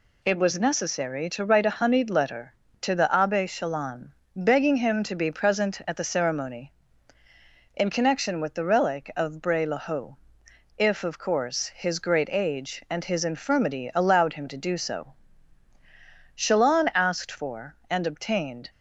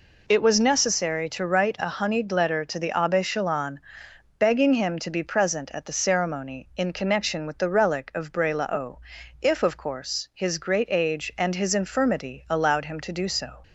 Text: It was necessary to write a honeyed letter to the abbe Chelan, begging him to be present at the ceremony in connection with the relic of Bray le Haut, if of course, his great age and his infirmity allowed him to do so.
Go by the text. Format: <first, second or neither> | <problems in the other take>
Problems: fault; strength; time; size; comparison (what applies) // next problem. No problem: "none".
second | goes on to say "Chelan asked for and obtained"; strong; from 16.3 s on; 2.3 s long